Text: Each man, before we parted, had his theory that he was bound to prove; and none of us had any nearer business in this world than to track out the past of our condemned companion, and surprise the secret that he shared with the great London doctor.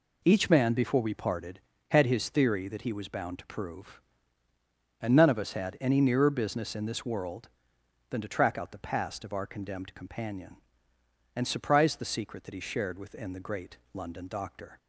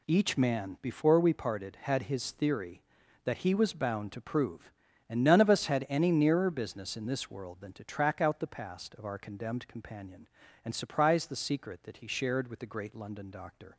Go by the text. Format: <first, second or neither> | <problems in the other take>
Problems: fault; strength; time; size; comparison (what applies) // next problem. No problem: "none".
second | says "within" for "with"; at 12.9 s // pauses between "great" and "London"; slight; at 13.7 s; 0.16 s long